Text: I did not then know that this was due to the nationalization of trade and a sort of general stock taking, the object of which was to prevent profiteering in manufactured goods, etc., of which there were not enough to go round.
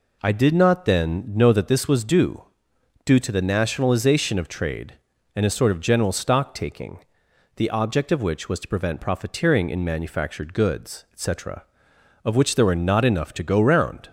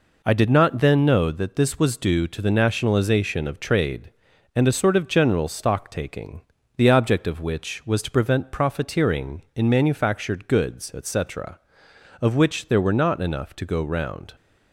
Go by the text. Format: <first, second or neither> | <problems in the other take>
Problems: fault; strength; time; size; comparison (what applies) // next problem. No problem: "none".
second | says "due" twice; at 3.0 s